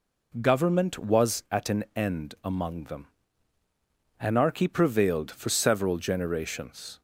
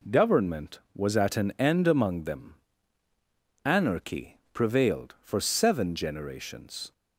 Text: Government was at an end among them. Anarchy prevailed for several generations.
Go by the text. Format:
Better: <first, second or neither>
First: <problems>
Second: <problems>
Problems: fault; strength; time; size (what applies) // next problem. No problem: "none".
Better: first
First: none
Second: says "seven" for "several"; at 5.3 s